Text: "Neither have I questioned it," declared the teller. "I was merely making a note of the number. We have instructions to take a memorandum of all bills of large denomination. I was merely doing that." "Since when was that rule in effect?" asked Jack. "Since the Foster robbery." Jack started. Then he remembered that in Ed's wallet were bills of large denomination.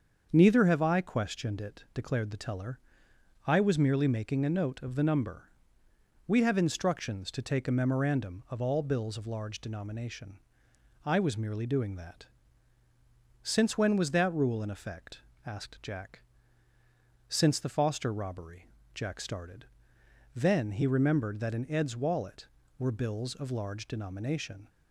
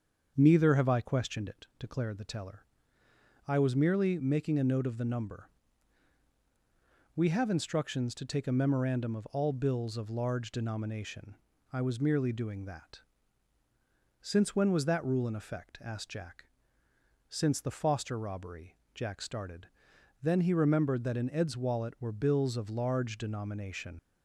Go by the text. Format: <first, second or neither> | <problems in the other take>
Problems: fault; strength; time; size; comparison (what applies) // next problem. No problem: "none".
first | starts louder than the rest; until 1.3 s; 7 dB; also in the first // leaves "denomination" unfinished; at 23.9 s; 65 ms